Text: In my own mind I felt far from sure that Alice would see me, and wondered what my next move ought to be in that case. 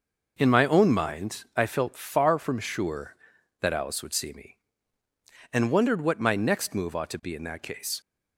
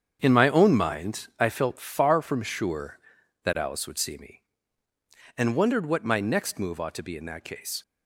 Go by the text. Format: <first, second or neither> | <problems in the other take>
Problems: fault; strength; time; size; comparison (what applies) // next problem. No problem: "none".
first | gets quieter; strong; throughout; 9.5 dB